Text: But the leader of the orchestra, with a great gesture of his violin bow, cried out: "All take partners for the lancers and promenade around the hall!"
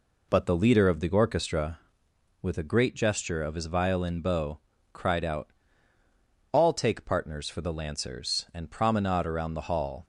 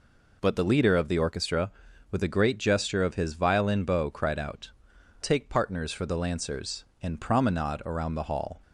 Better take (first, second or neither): first